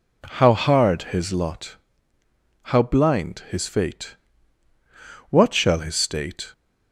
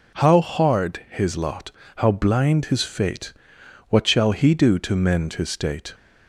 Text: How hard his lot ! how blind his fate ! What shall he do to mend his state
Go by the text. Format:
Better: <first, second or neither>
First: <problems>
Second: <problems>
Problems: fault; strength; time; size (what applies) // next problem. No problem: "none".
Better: second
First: skips "he do to mend"; at 5.7 s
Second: none